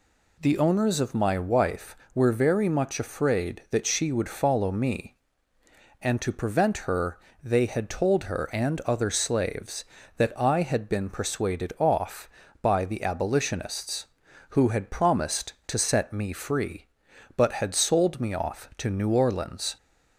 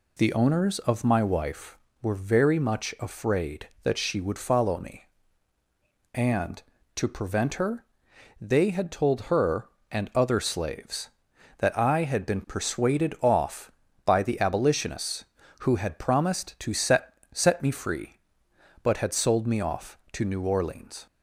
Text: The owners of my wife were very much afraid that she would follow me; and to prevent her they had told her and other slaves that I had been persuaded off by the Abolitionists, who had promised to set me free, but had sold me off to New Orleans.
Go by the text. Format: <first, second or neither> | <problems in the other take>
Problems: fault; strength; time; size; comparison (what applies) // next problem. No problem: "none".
first | pauses between "her" and "they"; noticeable; at 7.8 s; 0.56 s long; slight in the first // says "set" twice; at 17.3 s